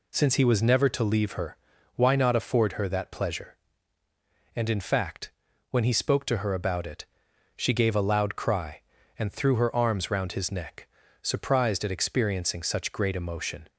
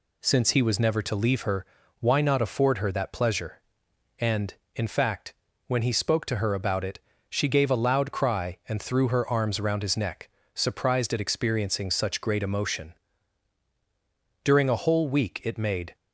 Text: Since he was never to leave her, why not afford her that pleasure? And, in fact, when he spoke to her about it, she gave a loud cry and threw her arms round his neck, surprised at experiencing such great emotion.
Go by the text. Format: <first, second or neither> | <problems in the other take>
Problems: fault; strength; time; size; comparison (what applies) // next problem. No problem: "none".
first | goes on to say "During a whole week it made"; from 14.4 s on; 1.5 s long